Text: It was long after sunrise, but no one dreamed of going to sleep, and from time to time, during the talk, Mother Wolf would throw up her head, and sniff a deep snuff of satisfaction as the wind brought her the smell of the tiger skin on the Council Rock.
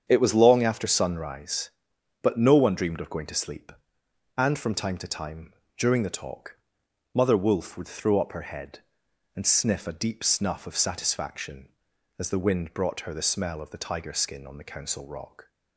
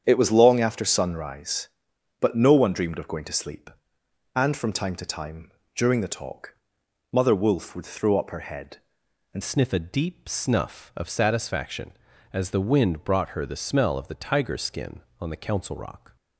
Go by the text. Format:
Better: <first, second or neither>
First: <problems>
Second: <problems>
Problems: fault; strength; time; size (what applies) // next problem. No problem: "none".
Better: first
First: starts louder than the rest; strong; until 1.0 s; 7.5 dB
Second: starts louder than the rest; strong; until 1.0 s; 8 dB // changes voice at "sniff"; from 9.4 s on; 6.7 s long